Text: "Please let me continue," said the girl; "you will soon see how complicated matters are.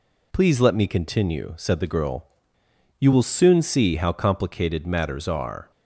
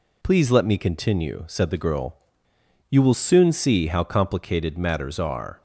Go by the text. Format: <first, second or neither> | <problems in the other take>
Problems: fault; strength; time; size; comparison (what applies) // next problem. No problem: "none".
neither | none